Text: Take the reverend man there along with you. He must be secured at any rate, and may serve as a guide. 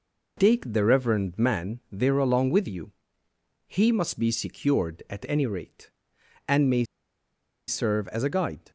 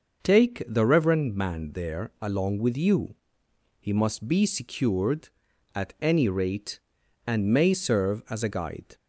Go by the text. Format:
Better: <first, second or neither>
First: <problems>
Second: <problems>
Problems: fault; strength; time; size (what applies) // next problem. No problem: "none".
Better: second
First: pauses between "may" and "serve"; noticeable; at 6.8 s; 0.83 s long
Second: none